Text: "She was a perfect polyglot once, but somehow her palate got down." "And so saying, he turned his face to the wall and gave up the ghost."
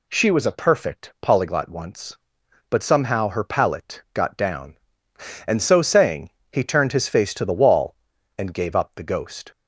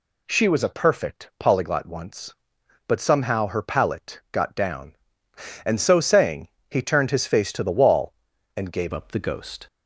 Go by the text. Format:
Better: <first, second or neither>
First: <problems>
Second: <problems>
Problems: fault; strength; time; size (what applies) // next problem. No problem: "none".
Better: first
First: none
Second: changes voice at "up"; from 8.9 s on; 0.7 s long